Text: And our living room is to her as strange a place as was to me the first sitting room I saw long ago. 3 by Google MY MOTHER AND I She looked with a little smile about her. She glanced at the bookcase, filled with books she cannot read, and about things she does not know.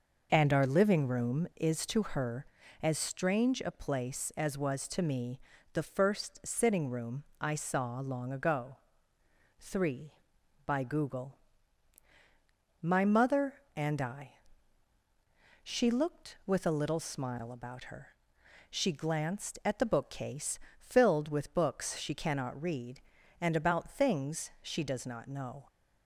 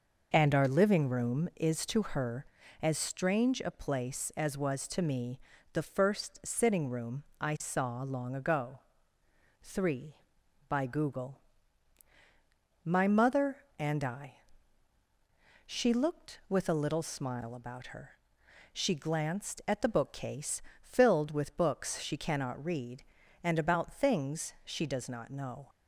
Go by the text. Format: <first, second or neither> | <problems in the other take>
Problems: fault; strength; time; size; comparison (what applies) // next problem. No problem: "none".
neither | pauses between "me" and "the"; slight; the same in both // pauses between "room" and "I"; slight; the same in both // pauses between "Google" and "MY"; strong; the same in both // pauses between "I" and "She"; strong; the same in both